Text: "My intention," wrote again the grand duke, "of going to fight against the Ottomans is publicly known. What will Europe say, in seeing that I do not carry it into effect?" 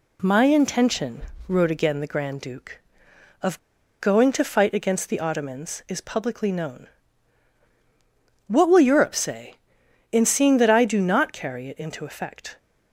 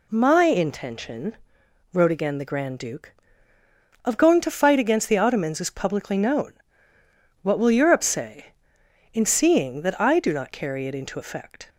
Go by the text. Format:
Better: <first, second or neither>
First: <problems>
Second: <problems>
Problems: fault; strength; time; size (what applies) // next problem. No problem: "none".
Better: second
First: pauses between "of" and "going"; at 3.5 s; 0.41 s long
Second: none